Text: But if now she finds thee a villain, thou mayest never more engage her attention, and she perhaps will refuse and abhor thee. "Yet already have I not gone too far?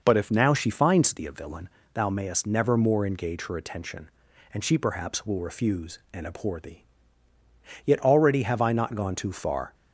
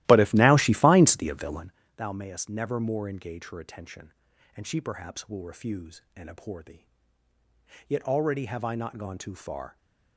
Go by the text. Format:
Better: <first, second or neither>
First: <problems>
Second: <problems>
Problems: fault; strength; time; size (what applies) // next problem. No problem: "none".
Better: first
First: none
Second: starts louder than the rest; strong; until 1.7 s; 16 dB